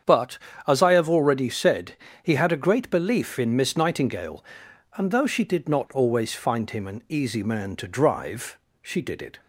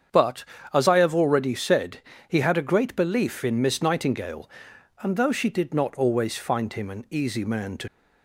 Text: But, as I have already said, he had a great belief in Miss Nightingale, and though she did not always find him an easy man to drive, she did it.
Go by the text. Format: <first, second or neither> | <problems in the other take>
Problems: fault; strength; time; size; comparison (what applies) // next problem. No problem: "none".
first | starts louder than the rest; strong; until 1.4 s; 7.5 dB; strong in the first // stops before "drive she did it"; at 7.8 s